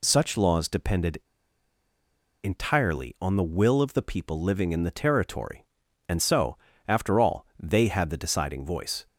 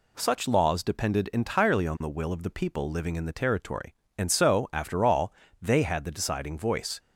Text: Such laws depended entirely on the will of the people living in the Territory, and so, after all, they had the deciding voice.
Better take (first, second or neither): second